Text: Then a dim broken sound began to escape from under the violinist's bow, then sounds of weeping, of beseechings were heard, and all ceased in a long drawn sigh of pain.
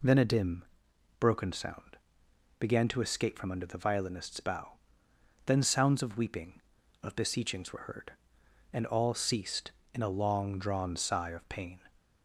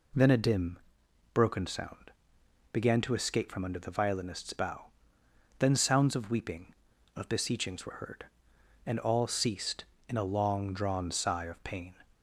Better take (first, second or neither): neither